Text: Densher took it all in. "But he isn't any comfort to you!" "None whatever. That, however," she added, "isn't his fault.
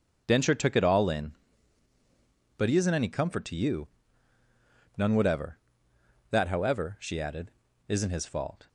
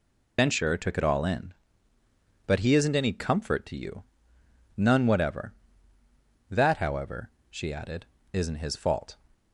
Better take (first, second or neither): first